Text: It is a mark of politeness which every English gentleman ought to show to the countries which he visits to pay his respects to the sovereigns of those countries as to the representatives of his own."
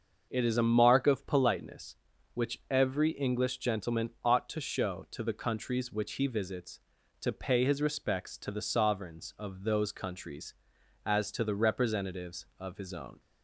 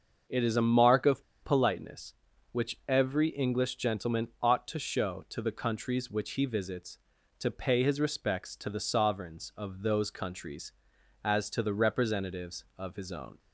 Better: first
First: starts louder than the rest; until 1.3 s; 6.5 dB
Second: starts louder than the rest; until 1.4 s; 6.5 dB // pauses between "of" and "politeness"; slight; at 1.2 s; 0.20 s long

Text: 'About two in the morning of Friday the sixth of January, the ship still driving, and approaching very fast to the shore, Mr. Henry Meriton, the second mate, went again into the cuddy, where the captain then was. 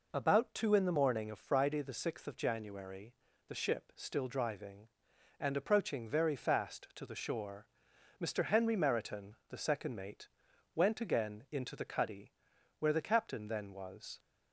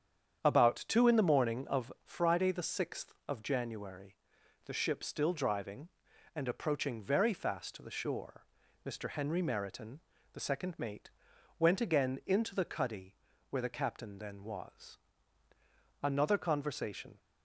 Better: first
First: none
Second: starts louder than the rest; strong; until 1.4 s; 8.5 dB // goes on to say "Another conversation"; noticeable; from 16.0 s on; 1.1 s long

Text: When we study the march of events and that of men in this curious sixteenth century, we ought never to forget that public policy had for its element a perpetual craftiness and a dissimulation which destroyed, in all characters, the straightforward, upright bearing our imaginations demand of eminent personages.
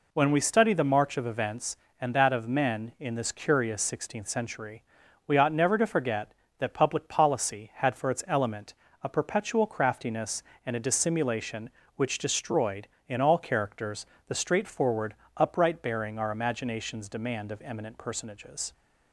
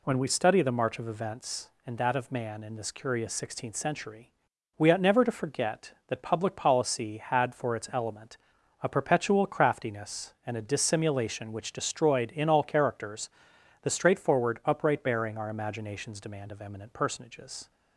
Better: first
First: pauses between "element" and "a"; slight; at 8.7 s; 0.28 s long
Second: says "man" for "men"; at 2.3 s // pauses between "element" and "a"; noticeable; at 8.3 s; 0.46 s long

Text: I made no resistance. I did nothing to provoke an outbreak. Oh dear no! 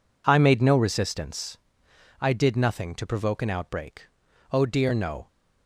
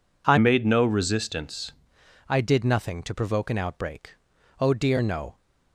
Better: first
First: none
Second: changes voice from "made" to "resistance"; from 0.3 to 1.7 s; 1.4 s long

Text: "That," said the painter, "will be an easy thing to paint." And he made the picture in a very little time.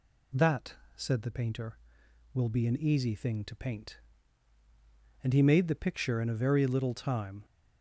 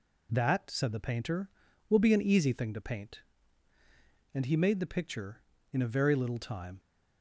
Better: second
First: gets louder; noticeable; throughout; 5 dB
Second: none

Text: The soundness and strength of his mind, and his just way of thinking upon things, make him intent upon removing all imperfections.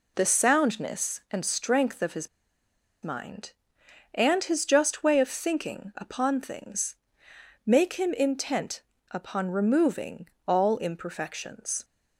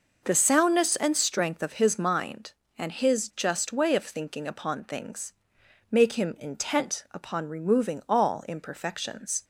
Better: second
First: pauses between "his" and "mind"; noticeable; at 2.2 s; 0.76 s long // pauses between "intent" and "upon"; slight; at 8.8 s; 0.30 s long // pauses between "removing" and "all"; slight; at 10.2 s; 0.18 s long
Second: none

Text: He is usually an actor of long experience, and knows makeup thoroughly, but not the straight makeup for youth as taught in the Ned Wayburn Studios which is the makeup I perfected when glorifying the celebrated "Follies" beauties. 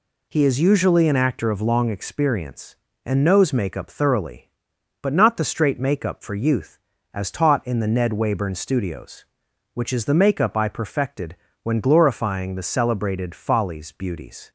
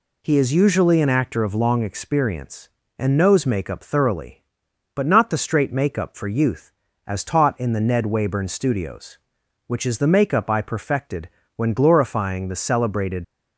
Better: first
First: pauses between "perfected" and "when"; slight; at 11.3 s; 0.26 s long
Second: pauses between "perfected" and "when"; slight; at 11.2 s; 0.26 s long // stops before "Follies beauties"; at 13.2 s

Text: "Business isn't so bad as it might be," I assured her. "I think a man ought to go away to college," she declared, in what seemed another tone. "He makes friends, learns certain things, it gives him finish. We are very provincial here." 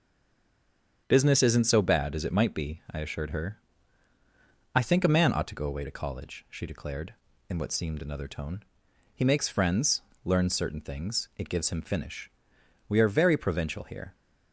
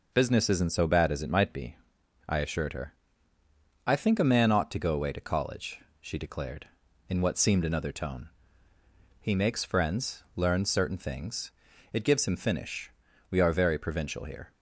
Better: second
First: stays silent before the first word; until 1.0 s; 1.0 s long // starts louder than the rest; strong; until 2.0 s; 7.5 dB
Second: none

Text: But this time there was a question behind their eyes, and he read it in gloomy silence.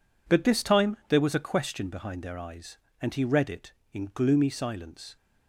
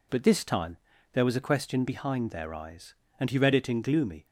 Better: first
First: none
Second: pauses between "time" and "there"; slight; at 0.7 s; 0.36 s long // stops before "silence"; at 4.2 s

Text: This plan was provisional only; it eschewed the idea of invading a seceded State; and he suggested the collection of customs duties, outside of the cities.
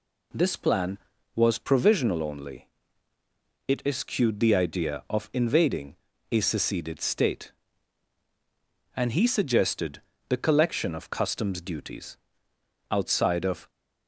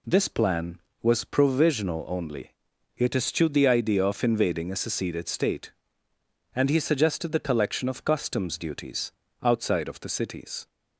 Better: second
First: pauses between "invading" and "a"; slight; at 5.9 s; 0.36 s long // pauses between "suggested" and "the"; slight; at 10.0 s; 0.26 s long // stops before "the cities"; at 13.6 s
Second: none

